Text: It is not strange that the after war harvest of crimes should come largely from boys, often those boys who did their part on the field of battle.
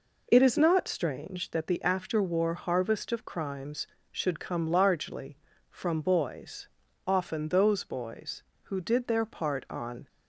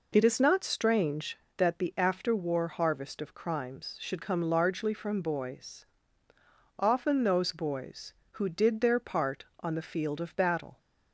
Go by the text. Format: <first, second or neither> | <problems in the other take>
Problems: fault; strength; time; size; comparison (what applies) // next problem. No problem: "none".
second | stops before "the field of battle"; at 10.0 s